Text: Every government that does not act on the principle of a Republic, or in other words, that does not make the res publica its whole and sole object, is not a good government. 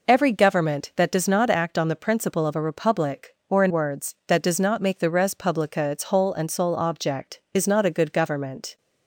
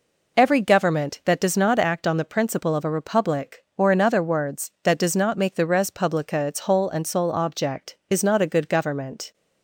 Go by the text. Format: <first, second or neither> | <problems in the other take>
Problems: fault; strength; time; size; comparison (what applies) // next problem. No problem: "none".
second | skips "other"; at 3.7 s